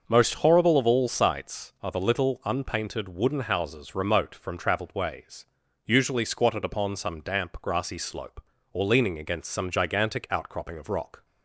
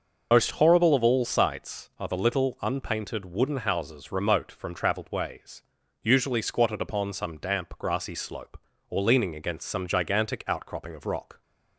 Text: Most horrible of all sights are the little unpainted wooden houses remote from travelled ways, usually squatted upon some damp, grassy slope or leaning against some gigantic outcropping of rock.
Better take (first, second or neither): first